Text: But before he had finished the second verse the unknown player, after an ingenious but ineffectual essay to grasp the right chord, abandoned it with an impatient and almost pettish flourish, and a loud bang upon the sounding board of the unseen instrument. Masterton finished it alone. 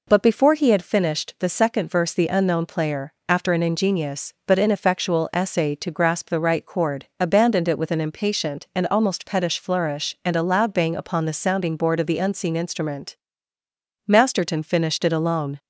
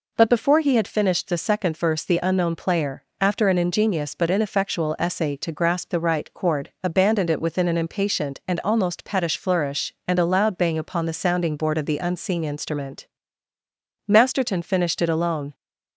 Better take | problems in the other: first | says "within" for "with"; at 7.4 s

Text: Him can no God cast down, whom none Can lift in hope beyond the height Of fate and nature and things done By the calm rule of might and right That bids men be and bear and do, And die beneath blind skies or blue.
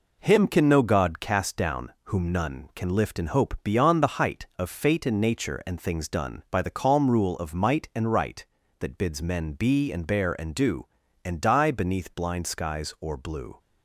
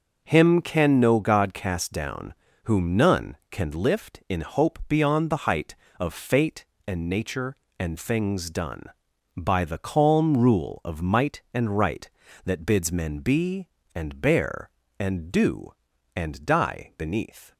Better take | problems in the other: first | stops before "blind skies or blue"; at 17.5 s

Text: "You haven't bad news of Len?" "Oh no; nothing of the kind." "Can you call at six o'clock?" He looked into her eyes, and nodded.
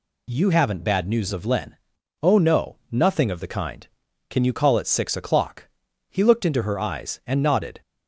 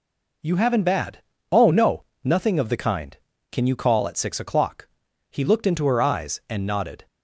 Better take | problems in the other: first | skips "news of Len"; at 1.3 s

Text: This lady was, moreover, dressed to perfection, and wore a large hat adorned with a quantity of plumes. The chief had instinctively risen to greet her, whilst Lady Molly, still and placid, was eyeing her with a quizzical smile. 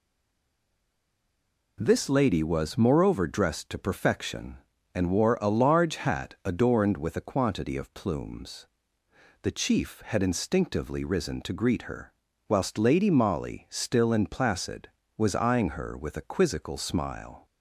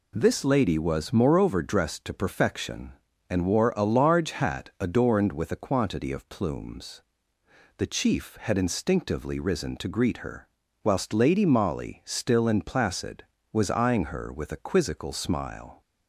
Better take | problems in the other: second | stays silent before the first word; noticeable; until 1.7 s; 1.7 s long

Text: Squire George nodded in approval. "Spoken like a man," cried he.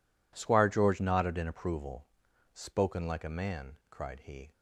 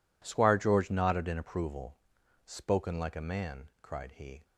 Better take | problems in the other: neither | none

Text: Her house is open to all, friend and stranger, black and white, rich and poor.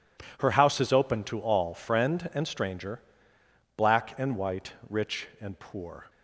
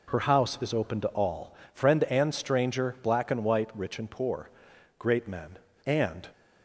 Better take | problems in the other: first | goes on to say "Great men and"; from 4.9 s on; 1.3 s long

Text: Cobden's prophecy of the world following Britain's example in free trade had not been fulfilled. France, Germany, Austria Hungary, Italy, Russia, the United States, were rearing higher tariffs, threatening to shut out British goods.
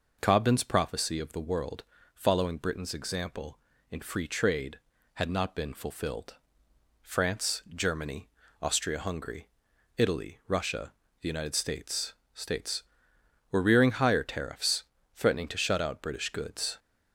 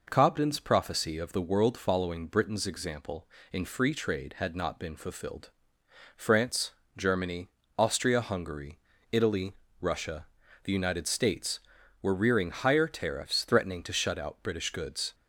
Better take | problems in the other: second | pauses between "world" and "following"; slight; at 1.8 s; 0.30 s long // says "States" twice; at 12.3 s

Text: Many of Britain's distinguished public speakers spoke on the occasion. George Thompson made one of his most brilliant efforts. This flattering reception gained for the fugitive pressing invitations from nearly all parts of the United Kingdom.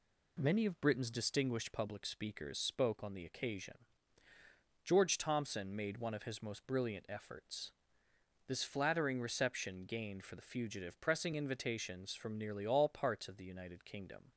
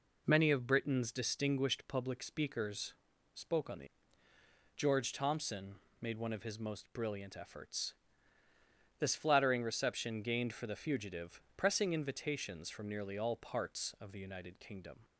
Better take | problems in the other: first | pauses between "speakers" and "spoke"; at 2.9 s; 0.42 s long // skips "occasion"; at 4.3 s // pauses between "Thompson" and "made"; slight; at 5.7 s; 0.26 s long // pauses between "fugitive" and "pressing"; slight; at 11.4 s; 0.16 s long

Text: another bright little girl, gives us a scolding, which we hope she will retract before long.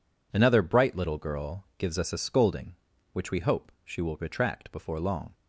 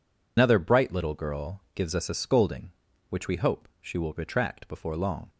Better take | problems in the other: first | loses the start of "another"; at 0.3 s; 85 ms

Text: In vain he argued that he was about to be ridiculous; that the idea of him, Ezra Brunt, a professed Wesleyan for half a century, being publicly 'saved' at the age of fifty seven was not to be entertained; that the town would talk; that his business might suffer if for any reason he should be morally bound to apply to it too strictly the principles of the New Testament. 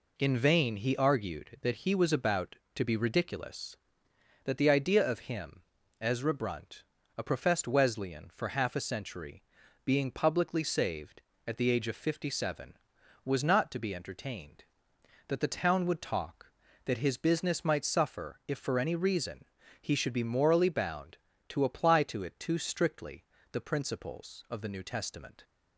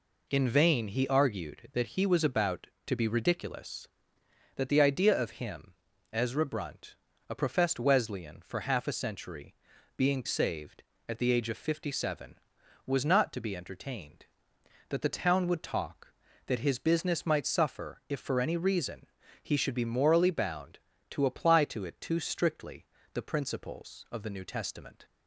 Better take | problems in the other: first | skips "publicly"; at 10.2 s // pauses between "reason" and "he"; at 19.0 s; 0.38 s long; also in the first // pauses between "strictly" and "the"; slight; at 22.8 s; 0.26 s long; slight in the first

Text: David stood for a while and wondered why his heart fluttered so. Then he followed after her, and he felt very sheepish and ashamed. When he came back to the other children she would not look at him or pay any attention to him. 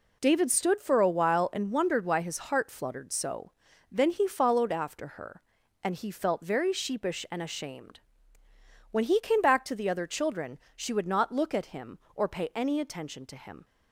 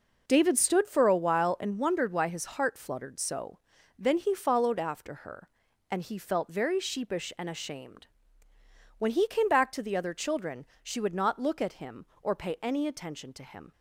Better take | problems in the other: first | starts louder than the rest; noticeable; until 1.2 s; 5 dB // pauses between "children" and "she"; slight; at 10.6 s; 0.16 s long; slight in the first

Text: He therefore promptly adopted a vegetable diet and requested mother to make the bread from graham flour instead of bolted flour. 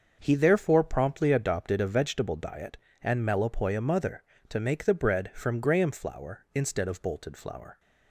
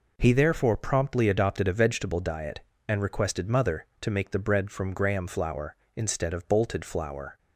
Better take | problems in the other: second | starts louder than the rest; until 1.2 s; 6.5 dB // says "melopoia" for "requested"; at 3.2 s

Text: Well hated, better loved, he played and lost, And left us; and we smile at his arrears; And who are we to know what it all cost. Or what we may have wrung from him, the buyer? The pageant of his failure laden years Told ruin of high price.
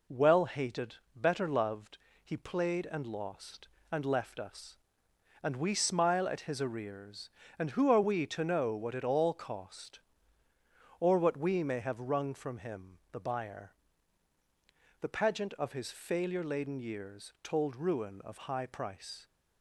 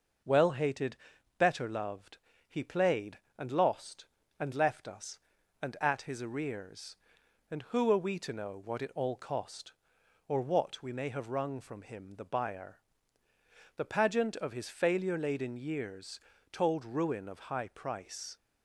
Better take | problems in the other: first | skips "we smile"; at 5.7 s // pauses between "years" and "Told"; slight; at 16.1 s; 0.32 s long

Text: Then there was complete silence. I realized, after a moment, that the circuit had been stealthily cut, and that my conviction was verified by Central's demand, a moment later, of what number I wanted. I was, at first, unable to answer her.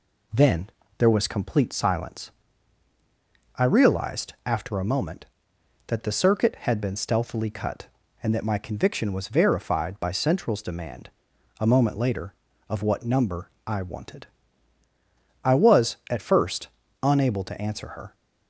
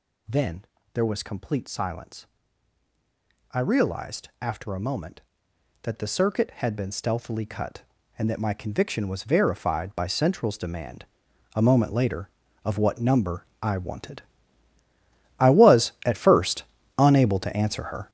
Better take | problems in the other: first | gets louder; strong; throughout; 9.5 dB // pauses between "Then" and "there"; slight; at 0.6 s; 0.28 s long; slight in the first // pauses between "number" and "I"; slight; at 13.4 s; 0.16 s long; slight in the first

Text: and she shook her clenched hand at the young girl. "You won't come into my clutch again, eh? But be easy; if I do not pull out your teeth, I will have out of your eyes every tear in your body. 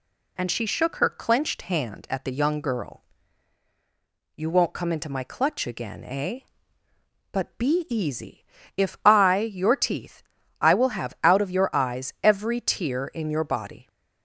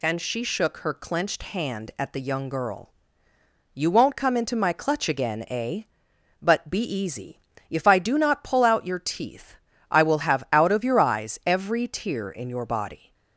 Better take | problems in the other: second | skips "do not pull out"; at 9.4 s

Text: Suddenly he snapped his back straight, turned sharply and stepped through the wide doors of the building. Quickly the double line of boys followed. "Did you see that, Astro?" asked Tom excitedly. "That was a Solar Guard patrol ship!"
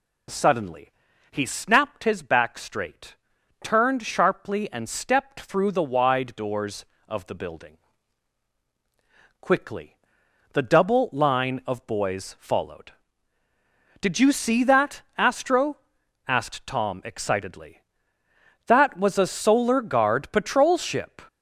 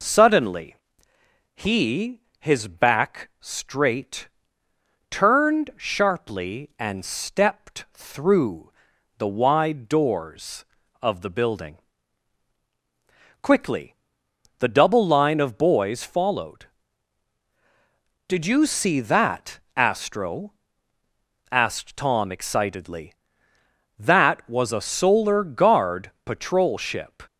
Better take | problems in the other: first | pauses between "Suddenly" and "he"; noticeable; at 0.7 s; 0.80 s long; also in the first // skips "snapped"; at 2.3 s // pauses between "through" and "the"; noticeable; at 8.7 s; 0.48 s long // pauses between "Quickly" and "the"; noticeable; at 13.9 s; 0.64 s long; noticeable in the first

